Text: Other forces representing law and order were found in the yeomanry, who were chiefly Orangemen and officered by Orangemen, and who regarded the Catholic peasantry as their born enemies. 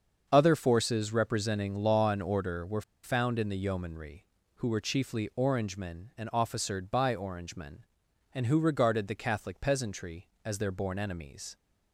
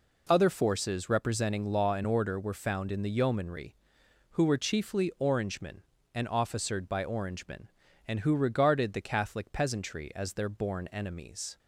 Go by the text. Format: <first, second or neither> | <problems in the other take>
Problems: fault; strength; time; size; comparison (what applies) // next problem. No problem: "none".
second | starts louder than the rest; until 1.3 s; 7 dB // pauses between "were" and "found"; slight; at 2.8 s; 0.21 s long